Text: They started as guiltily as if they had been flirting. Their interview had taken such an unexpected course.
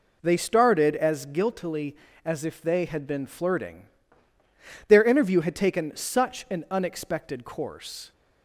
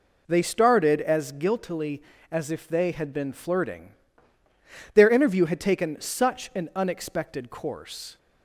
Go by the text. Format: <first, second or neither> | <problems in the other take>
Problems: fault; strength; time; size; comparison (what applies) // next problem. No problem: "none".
neither | none